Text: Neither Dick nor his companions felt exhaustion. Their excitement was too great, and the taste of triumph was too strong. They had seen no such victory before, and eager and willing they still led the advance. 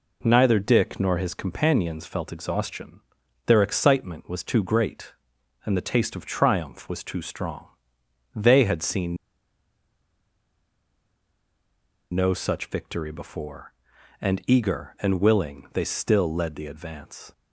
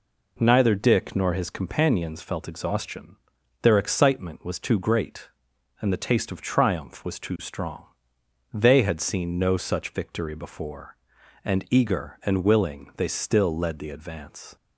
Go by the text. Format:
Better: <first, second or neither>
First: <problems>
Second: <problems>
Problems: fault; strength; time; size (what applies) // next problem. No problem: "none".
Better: second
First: pauses between "seen" and "no"; strong; at 9.1 s; 2.9 s long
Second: none